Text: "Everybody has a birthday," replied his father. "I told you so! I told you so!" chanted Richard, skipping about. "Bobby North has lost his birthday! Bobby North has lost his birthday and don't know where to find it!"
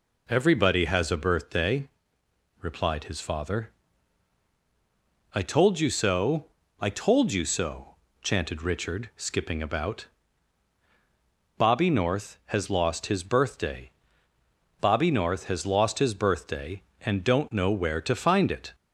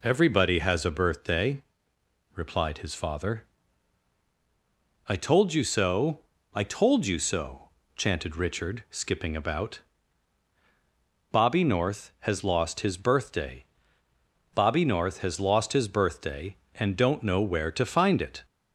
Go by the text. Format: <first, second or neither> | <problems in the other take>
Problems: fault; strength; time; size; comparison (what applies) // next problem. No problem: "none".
neither | none